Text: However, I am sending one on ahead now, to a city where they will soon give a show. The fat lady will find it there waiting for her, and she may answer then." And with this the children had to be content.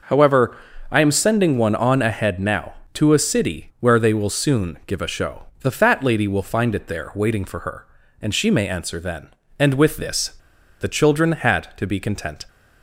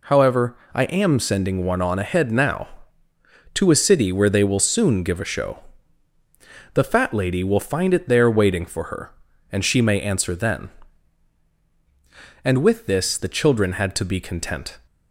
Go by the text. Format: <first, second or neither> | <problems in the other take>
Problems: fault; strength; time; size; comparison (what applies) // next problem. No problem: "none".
second | pauses between "this" and "the"; noticeable; at 10.3 s; 0.49 s long